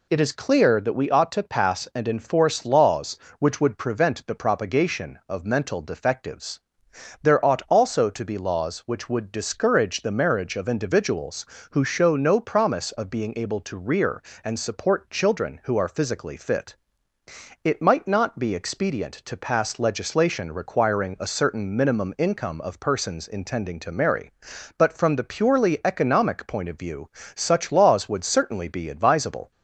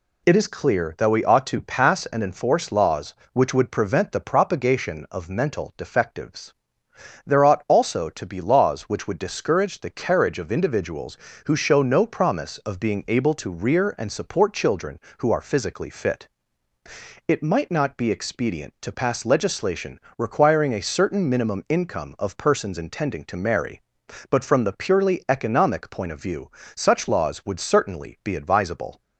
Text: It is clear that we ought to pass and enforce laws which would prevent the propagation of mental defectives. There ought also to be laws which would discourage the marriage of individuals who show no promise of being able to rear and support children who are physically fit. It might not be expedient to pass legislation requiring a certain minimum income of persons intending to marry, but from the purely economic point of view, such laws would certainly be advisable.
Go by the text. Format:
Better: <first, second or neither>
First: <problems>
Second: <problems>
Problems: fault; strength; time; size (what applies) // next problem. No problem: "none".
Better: first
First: none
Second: says "carriage" for "marriage"; at 9.8 s // pauses between "legislation" and "requiring"; slight; at 19.9 s; 0.18 s long